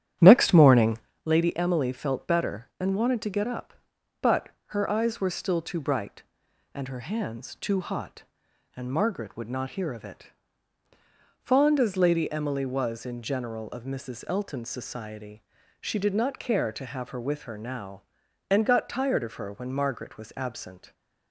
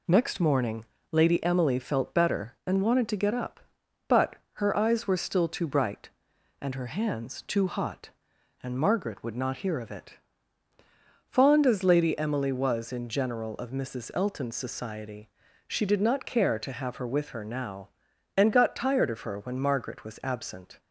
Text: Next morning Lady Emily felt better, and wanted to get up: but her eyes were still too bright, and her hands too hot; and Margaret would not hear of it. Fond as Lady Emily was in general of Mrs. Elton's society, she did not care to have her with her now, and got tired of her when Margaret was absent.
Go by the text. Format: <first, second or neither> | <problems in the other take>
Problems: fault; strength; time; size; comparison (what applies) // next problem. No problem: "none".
second | starts louder than the rest; strong; until 1.1 s; 10.5 dB // pauses between "morning" and "Lady"; slight; at 0.9 s; 0.28 s long; slight in the second // pauses between "but" and "her"; slight; at 4.4 s; 0.20 s long; slight in the second